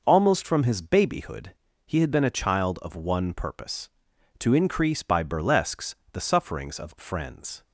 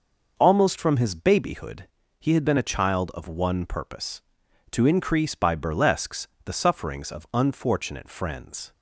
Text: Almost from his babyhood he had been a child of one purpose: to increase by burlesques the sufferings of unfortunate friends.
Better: second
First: pauses between "babyhood" and "he"; slight; at 1.5 s; 0.32 s long // pauses between "burlesques" and "the"; slight; at 5.9 s; 0.16 s long // skips "unfortunate"; at 6.9 s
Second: pauses between "babyhood" and "he"; slight; at 1.8 s; 0.32 s long // pauses between "burlesques" and "the"; slight; at 6.2 s; 0.16 s long

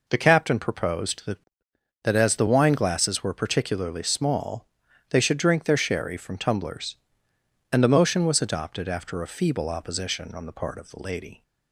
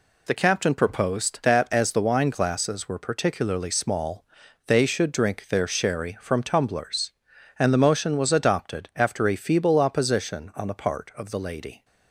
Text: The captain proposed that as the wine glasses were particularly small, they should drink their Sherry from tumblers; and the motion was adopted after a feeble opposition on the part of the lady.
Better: second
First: says "that" twice; at 2.0 s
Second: none

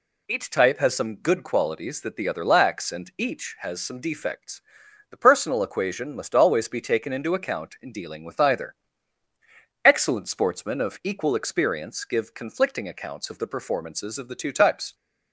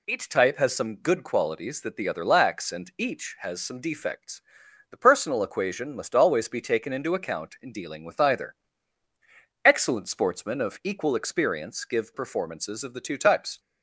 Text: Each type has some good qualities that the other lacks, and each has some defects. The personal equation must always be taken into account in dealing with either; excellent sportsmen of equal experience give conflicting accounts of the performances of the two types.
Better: first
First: none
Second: skips "conflicting accounts of the"; at 12.1 s

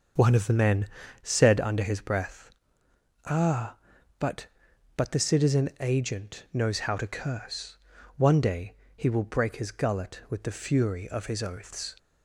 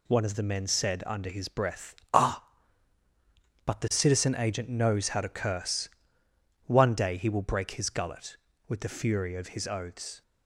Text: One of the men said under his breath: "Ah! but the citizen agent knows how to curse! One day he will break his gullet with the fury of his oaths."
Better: second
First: starts louder than the rest; until 1.5 s; 6.5 dB // pauses between "men" and "said"; slight; at 0.8 s; 0.34 s long // says "but" twice; at 4.9 s // pauses between "day" and "he"; slight; at 8.7 s; 0.20 s long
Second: none

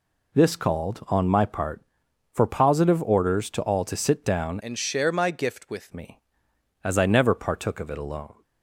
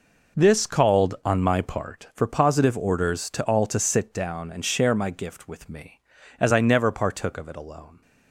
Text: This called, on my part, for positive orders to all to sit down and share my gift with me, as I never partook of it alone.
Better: second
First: changes voice from "and" to "with"; from 4.6 to 5.9 s; 1.3 s long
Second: none

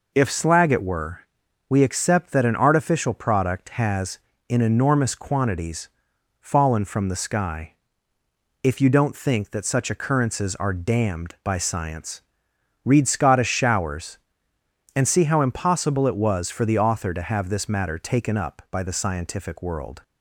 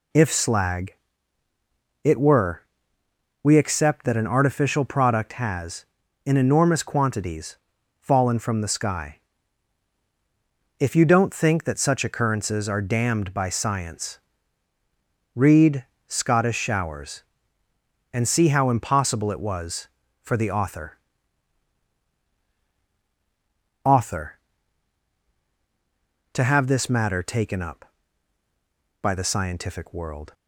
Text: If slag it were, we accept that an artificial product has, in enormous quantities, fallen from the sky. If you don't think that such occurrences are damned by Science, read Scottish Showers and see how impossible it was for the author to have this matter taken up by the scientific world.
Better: first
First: none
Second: pauses between "slag" and "it"; at 0.9 s; 1.0 s long // pauses between "read" and "Scottish"; slight; at 15.8 s; 0.22 s long // says "author" twice; at 23.8 s

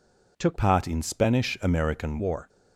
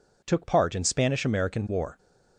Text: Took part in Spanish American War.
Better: second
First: changes voice from "part" to "American"; from 0.5 to 2.1 s; 1.6 s long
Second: none

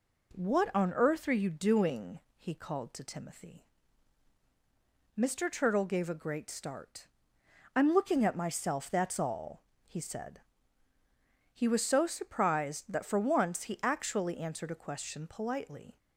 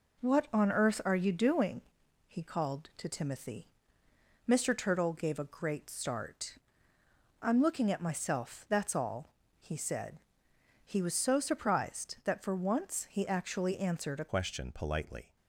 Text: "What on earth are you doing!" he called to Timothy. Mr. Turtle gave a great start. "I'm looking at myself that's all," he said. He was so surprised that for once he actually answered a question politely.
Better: first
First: none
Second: changes voice at "question"; from 14.2 s on; 1.1 s long

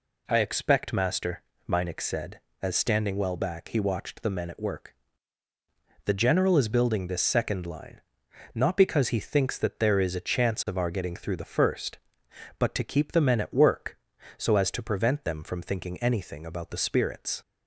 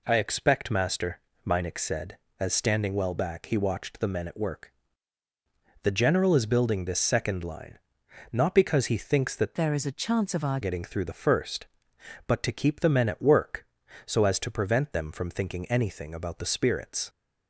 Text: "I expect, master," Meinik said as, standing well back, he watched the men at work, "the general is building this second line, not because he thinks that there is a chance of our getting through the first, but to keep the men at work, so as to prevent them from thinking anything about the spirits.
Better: first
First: none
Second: changes voice from "there" to "our"; from 9.5 to 10.5 s; 1.0 s long

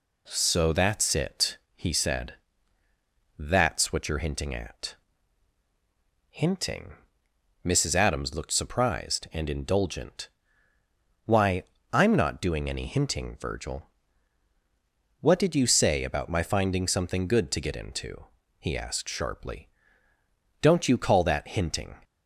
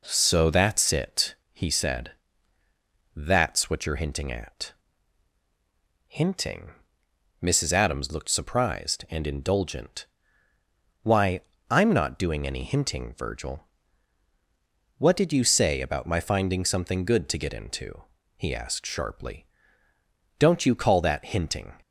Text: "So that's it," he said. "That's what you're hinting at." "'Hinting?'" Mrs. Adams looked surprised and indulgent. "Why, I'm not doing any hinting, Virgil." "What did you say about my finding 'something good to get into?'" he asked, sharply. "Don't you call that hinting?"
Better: first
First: none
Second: starts louder than the rest; noticeable; until 1.0 s; 4 dB

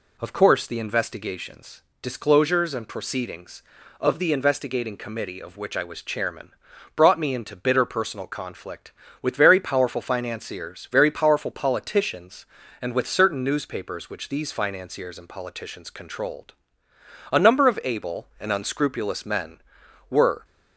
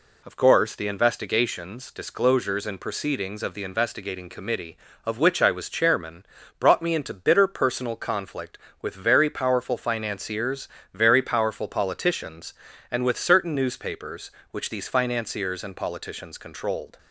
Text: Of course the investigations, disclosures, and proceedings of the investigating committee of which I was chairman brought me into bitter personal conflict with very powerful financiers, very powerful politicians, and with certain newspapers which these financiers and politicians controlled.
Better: second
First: pauses between "chairman" and "brought"; at 6.5 s; 0.44 s long // goes on to say "A number of able and unscrupulous men were"; strong; from 17.3 s on; 3.1 s long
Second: pauses between "chairman" and "brought"; slight; at 6.2 s; 0.32 s long

